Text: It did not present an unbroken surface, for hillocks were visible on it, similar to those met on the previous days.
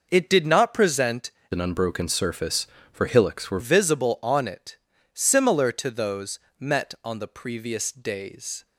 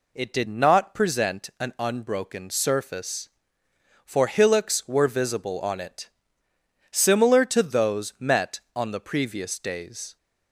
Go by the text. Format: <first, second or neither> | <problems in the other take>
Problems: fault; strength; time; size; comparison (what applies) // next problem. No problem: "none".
second | changes voice from "an" to "were"; from 1.5 to 3.5 s; 2.0 s long // pauses between "those" and "met"; slight; at 6.3 s; 0.18 s long